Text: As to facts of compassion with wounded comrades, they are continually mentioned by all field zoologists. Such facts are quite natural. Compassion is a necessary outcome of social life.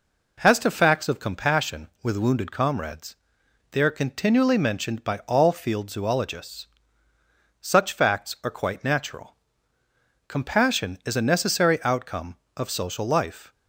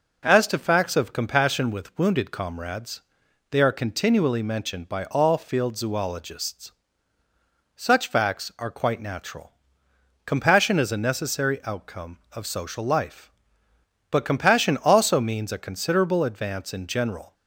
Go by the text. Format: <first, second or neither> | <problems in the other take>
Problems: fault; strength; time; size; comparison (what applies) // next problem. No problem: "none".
first | goes on to say "But compassion also means a considerable advance in general"; strong; from 14.0 s on; 3.2 s long